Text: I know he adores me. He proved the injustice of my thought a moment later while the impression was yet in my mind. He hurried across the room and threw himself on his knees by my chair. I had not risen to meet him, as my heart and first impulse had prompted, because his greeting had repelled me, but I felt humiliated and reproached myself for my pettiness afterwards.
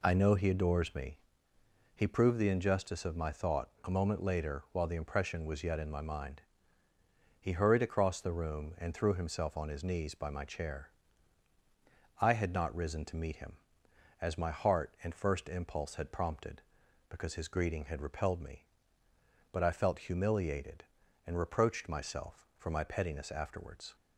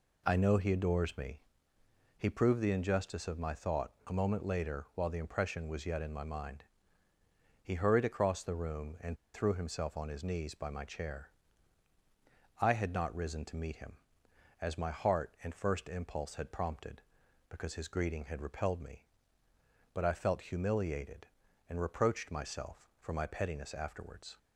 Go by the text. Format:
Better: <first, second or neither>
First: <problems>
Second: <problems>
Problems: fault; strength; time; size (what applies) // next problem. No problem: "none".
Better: first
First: pauses between "thought" and "a"; slight; at 3.6 s; 0.16 s long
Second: pauses between "thought" and "a"; slight; at 3.9 s; 0.16 s long // pauses between "and" and "threw"; slight; at 9.1 s; 0.17 s long